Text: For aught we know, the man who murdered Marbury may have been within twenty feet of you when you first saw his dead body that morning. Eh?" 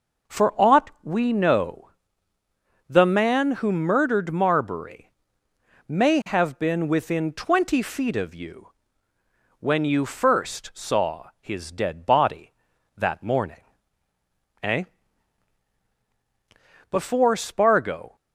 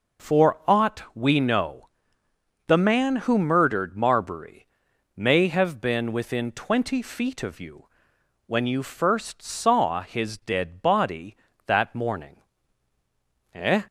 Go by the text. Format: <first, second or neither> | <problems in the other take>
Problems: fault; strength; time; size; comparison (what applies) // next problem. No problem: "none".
second | pauses between "Marbury" and "may"; noticeable; at 5.1 s; 0.76 s long; noticeable in the second // pauses between "you" and "when"; noticeable; at 8.6 s; 0.90 s long; noticeable in the second // goes on to say "Before Spargo"; noticeable; from 16.9 s on; 1.2 s long